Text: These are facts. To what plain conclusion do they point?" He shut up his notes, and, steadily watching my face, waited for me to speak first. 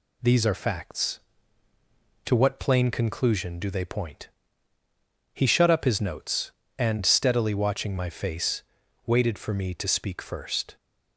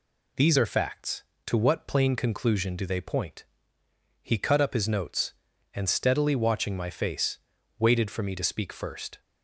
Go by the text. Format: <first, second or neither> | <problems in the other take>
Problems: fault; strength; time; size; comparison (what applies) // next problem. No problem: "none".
first | says "cut" for "shut"; at 4.3 s